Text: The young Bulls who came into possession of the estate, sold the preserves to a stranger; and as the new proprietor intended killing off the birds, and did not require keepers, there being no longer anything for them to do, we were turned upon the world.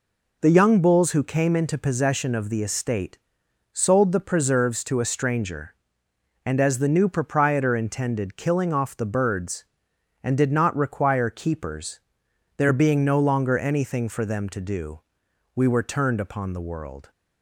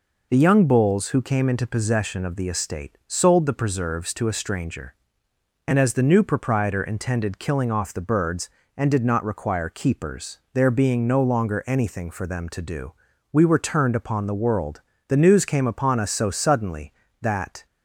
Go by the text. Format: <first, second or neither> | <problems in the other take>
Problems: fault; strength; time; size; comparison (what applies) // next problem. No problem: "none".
first | goes on to say "The news came upon us so suddenly that"; strong; from 15.0 s on; 2.5 s long